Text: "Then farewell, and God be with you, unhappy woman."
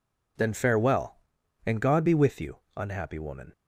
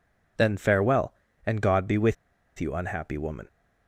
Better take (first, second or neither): first